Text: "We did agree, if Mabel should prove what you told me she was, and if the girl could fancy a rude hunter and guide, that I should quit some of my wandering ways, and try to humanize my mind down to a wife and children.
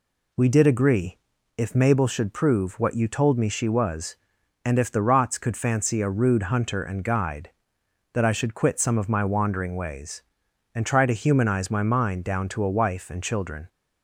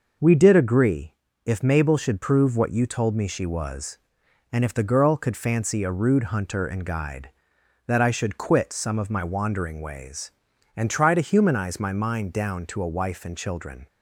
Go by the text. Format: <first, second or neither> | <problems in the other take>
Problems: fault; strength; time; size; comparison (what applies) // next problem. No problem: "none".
second | says "rots" for "girl"; at 5.0 s